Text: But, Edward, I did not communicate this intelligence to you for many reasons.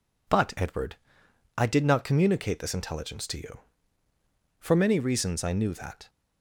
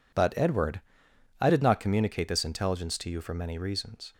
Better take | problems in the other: second | goes on to say "I knew that"; noticeable; from 5.4 s on; 0.64 s long

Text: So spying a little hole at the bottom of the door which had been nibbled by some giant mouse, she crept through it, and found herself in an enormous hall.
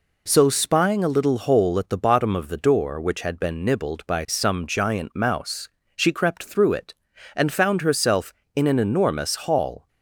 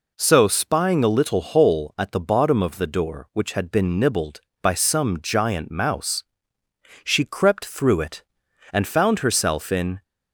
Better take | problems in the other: first | stops before "an enormous hall"; at 10.0 s

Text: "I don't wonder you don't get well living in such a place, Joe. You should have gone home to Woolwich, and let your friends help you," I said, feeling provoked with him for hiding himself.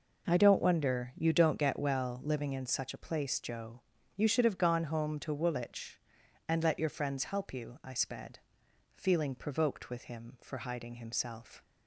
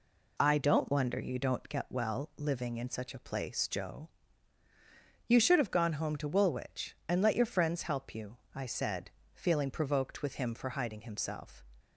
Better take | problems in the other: second | says "sped" for "said"; at 7.9 s

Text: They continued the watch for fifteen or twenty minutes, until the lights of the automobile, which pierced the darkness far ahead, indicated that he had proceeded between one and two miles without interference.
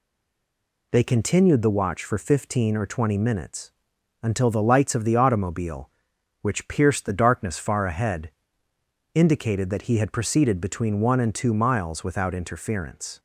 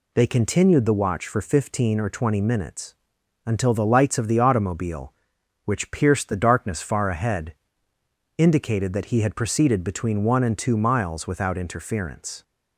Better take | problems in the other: second | stays silent before the first word; slight; until 0.9 s; 0.9 s long

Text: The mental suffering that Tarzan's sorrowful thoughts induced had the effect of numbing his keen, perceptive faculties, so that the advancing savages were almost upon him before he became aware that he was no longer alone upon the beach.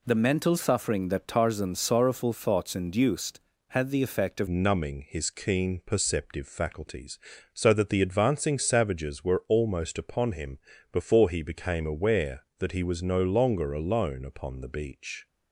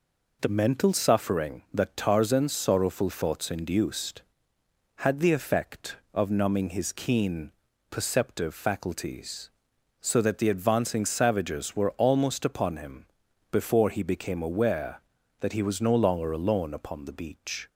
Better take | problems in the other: second | changes voice at "numbing"; from 4.4 s on; 10.8 s long // pauses between "him" and "before"; slight; at 10.5 s; 0.34 s long; also in the second

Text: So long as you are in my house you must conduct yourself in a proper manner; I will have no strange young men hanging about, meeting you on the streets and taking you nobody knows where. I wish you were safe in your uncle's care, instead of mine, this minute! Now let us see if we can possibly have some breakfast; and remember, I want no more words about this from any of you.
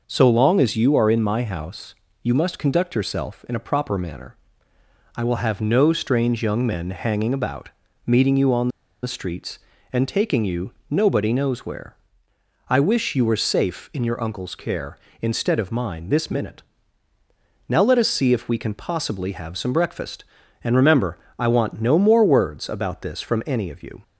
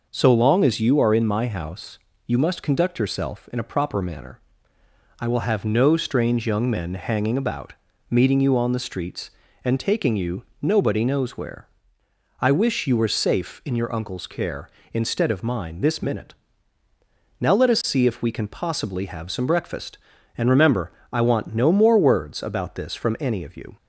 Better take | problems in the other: second | pauses between "house" and "you"; slight; at 1.9 s; 0.28 s long; slight in the second // pauses between "on" and "the"; slight; at 8.6 s; 0.34 s long // pauses between "you" and "nobody"; slight; at 10.7 s; 0.18 s long; slight in the second

